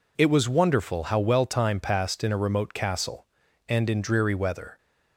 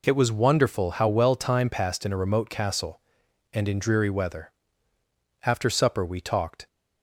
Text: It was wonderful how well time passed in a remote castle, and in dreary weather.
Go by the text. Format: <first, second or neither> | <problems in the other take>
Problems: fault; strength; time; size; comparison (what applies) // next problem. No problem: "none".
first | goes on to say "After supper we talked"; noticeable; from 5.4 s on; 1.2 s long